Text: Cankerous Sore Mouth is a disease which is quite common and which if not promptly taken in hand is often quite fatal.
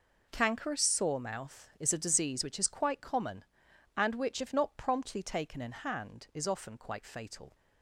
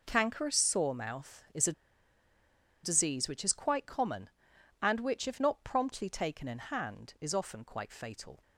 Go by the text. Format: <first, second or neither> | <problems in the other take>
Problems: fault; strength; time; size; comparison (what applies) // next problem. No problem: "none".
first | pauses between "a" and "disease"; at 1.7 s; 1.1 s long